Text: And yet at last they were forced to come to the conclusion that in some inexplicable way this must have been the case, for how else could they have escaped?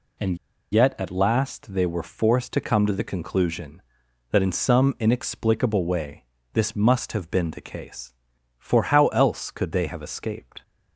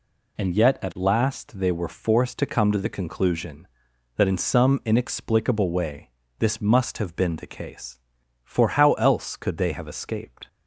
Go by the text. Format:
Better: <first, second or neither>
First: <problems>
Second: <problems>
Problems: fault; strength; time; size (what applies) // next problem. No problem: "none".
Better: second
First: pauses between "And" and "yet"; slight; at 0.3 s; 0.34 s long // pauses between "way" and "this"; slight; at 6.2 s; 0.30 s long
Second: pauses between "way" and "this"; slight; at 6.0 s; 0.30 s long